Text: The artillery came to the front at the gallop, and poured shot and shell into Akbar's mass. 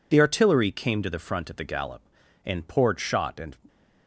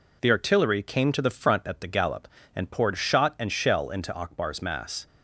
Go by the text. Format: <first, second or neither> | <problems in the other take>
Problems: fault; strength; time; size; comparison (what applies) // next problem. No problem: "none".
second | stops before "shell into Akbar's mass"; at 3.6 s